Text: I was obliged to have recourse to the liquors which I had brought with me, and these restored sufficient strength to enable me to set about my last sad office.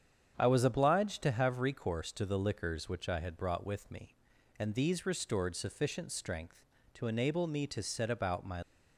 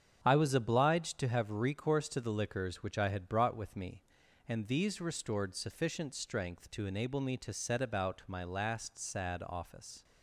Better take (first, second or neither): second